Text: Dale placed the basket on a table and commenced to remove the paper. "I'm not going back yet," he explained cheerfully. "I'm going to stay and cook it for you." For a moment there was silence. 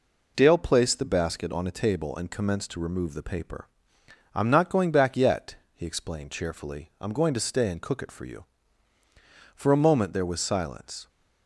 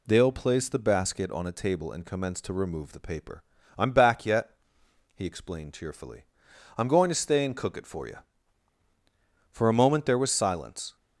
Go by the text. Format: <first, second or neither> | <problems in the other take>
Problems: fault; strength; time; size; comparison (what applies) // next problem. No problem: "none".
first | skips "not going"; at 3.9 s